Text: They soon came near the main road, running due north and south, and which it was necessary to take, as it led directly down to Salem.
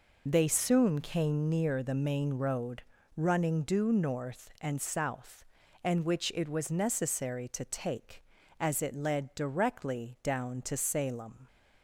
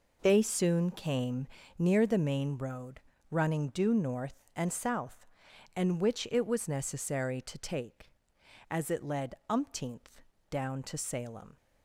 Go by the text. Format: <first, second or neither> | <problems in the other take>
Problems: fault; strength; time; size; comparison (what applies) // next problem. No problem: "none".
first | pauses between "came" and "near"; slight; at 1.4 s; 0.32 s long // says "umpteenth" for "directly"; at 9.4 s